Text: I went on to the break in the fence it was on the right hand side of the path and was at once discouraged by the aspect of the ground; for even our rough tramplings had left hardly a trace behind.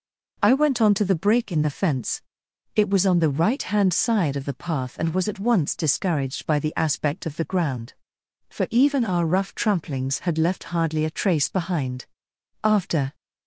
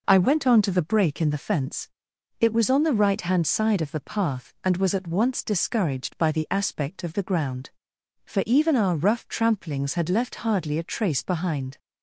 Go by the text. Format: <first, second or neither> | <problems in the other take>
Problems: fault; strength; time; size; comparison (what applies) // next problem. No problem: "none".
second | pauses between "fence" and "it"; noticeable; at 2.2 s; 0.56 s long; noticeable in the second // goes on to say "After"; from 12.6 s on; 0.52 s long